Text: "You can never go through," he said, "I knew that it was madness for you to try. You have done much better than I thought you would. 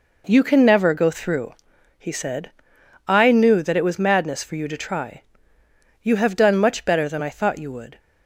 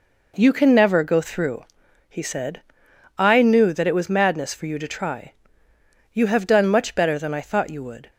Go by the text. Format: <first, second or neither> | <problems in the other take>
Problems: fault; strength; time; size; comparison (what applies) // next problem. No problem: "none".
neither | none